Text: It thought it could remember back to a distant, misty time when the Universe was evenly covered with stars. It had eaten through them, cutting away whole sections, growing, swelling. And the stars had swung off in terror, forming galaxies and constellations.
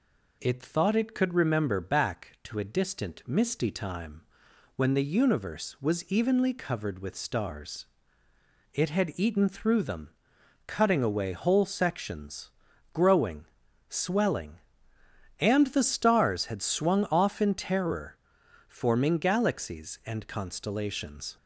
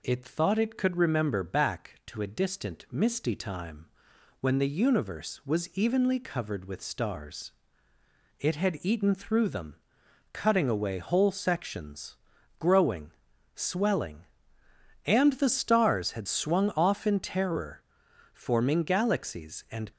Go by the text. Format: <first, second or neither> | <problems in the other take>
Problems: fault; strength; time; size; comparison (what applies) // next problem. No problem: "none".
first | pauses between "time" and "when"; noticeable; at 3.8 s; 0.54 s long; noticeable in the first // stops before "constellations"; at 19.9 s